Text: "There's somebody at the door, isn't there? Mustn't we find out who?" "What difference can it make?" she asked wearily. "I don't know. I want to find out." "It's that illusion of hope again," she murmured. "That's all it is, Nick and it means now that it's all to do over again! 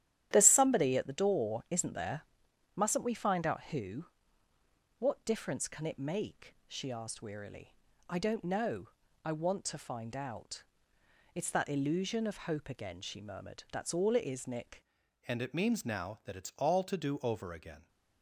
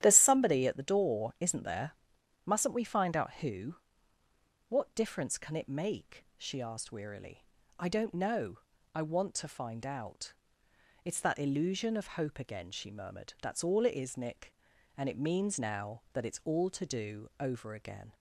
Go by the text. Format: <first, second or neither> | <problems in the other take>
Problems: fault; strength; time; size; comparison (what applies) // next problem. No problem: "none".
second | starts louder than the rest; strong; until 1.3 s; 11.5 dB; strong in the second // changes voice at "and"; from 15.2 s on; 2.6 s long